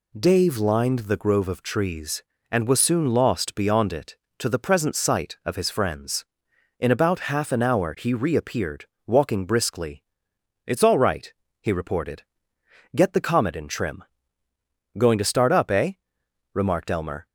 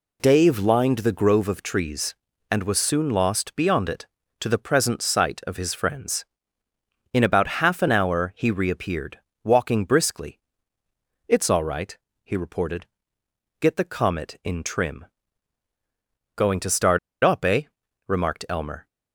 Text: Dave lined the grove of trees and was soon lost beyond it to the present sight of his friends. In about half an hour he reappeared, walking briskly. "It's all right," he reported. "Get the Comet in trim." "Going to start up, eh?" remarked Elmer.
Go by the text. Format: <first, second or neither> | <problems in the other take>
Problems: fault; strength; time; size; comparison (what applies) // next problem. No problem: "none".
first | pauses between "start" and "up"; slight; at 16.9 s; 0.25 s long